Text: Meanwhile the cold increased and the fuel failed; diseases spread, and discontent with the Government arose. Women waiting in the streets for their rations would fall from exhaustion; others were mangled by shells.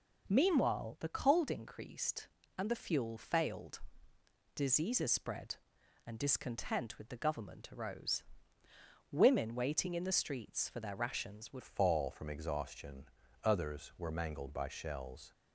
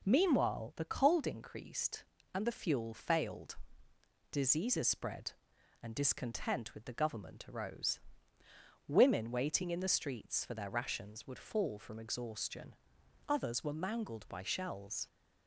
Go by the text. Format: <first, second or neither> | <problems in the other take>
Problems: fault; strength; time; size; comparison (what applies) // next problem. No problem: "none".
second | changes voice at "fall"; from 11.6 s on; 3.7 s long